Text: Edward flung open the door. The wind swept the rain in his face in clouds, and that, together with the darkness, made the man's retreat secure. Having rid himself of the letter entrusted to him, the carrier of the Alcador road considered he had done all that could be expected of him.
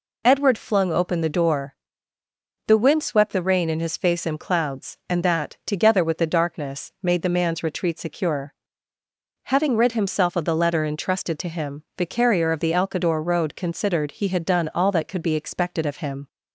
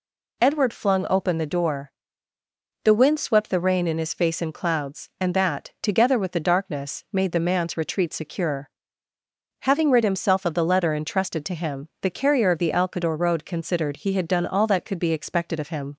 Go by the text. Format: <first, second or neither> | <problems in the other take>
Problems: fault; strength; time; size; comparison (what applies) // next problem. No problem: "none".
neither | none